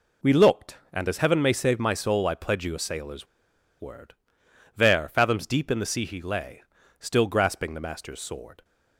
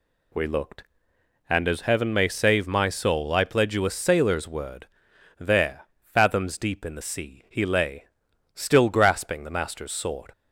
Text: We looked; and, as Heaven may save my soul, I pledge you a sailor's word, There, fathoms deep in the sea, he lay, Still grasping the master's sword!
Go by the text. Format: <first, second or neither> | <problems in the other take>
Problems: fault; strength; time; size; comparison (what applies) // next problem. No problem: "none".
second | pauses between "sailor's" and "word"; noticeable; at 3.2 s; 0.53 s long